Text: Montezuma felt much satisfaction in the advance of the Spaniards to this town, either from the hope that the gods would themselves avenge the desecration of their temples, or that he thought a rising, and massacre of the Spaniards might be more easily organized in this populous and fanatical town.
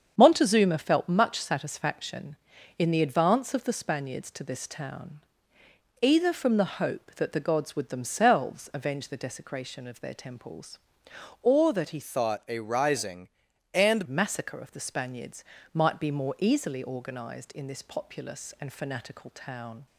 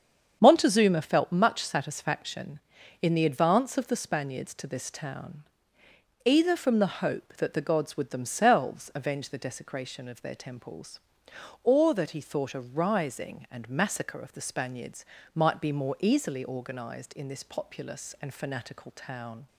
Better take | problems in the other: second | starts louder than the rest; strong; until 1.1 s; 7.5 dB; strong in the second // changes voice from "thought" to "and"; from 12.0 to 14.0 s; 2.0 s long // pauses between "Spaniards" and "might"; slight; at 15.4 s; 0.30 s long; slight in the second

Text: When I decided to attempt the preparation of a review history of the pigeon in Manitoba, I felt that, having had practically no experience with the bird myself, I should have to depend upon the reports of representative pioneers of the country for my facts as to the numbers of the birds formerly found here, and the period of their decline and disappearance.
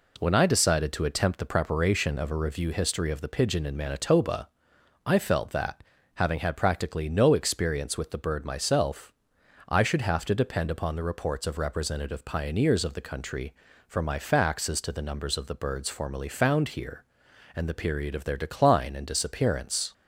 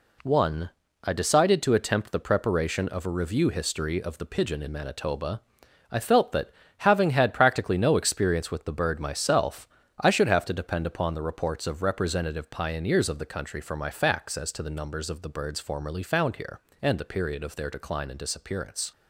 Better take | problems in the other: first | says "One" for "When"; at 0.2 s

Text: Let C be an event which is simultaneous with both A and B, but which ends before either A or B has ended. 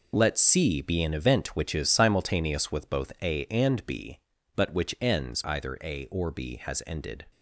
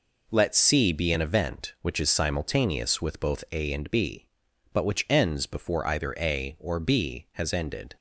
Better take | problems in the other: second | skips "before"; at 5.4 s

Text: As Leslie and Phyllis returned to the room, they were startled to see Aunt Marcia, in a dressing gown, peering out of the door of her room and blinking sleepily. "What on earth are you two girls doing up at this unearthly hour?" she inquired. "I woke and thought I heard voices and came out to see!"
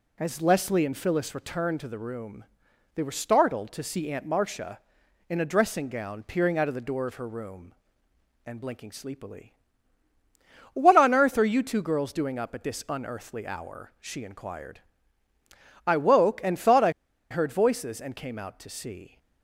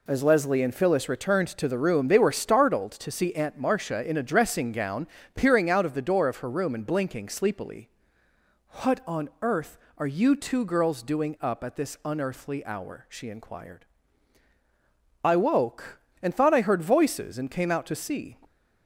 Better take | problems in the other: second | pauses between "I" and "heard"; at 16.8 s; 0.40 s long

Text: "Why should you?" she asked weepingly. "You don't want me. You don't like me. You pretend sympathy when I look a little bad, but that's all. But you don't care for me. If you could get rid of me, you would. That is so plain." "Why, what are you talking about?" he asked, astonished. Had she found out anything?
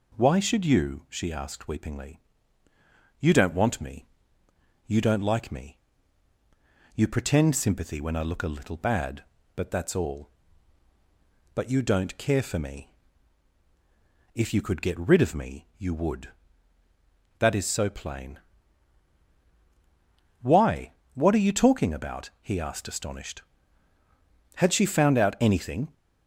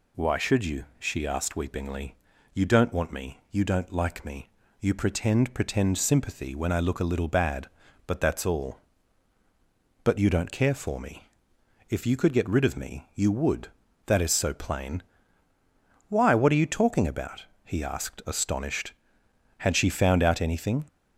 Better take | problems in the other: first | says "pretend" twice; at 5.5 s

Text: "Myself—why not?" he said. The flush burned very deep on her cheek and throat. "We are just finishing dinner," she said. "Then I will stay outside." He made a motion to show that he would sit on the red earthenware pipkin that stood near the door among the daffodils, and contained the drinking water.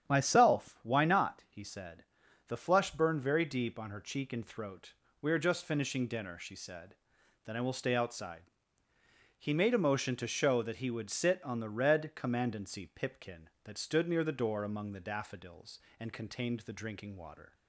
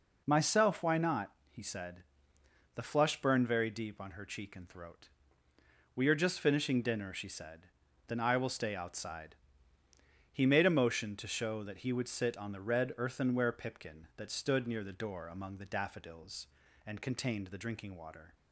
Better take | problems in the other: second | starts louder than the rest; strong; until 1.1 s; 9.5 dB // says "commandancy" for "earthenware"; at 12.1 s

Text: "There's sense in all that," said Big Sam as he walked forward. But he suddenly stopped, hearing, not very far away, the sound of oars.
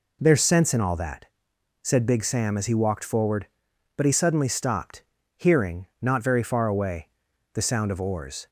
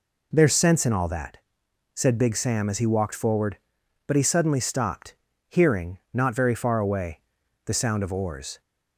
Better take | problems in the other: neither | none

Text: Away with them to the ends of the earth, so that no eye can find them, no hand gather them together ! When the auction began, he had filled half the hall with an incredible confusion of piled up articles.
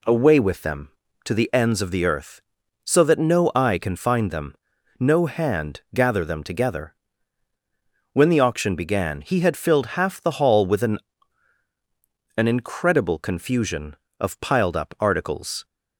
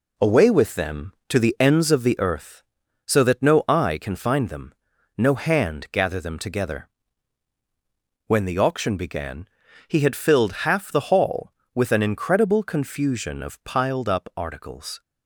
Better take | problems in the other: second | pauses between "hand" and "gather"; slight; at 5.7 s; 0.16 s long // says "an" twice; at 12.3 s

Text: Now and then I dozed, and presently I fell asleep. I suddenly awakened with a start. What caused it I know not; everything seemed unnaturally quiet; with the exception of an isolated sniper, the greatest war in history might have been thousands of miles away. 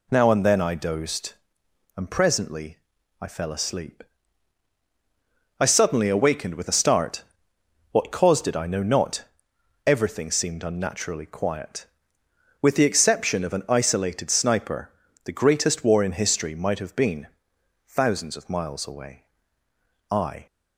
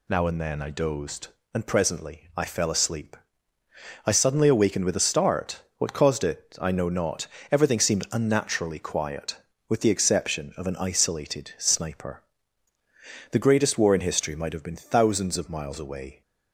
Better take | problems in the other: second | pauses between "presently" and "I"; at 2.7 s; 0.42 s long // pauses between "been" and "thousands"; noticeable; at 17.2 s; 0.60 s long // goes on to say "I"; slight; from 20.0 s on; 0.36 s long

